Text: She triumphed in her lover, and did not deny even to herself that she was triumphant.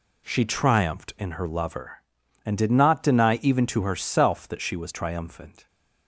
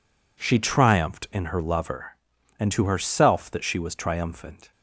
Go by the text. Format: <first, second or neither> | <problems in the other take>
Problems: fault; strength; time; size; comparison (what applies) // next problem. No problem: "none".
first | skips "did not deny even"; at 2.7 s